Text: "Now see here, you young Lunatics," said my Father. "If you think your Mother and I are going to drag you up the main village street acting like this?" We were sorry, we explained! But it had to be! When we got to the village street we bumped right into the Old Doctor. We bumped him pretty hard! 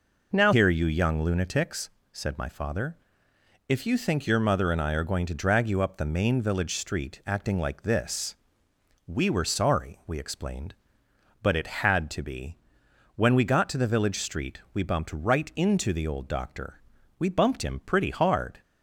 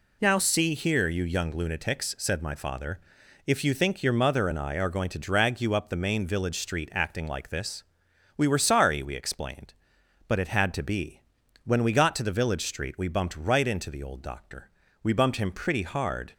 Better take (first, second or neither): second